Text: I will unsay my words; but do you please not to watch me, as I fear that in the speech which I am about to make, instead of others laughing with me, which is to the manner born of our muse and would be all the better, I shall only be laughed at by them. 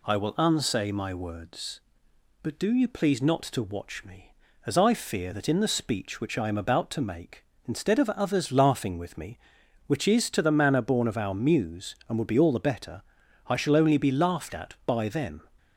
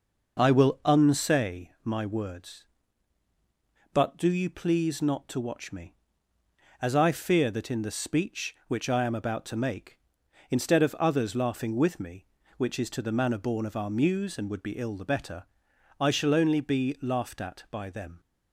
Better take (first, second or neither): first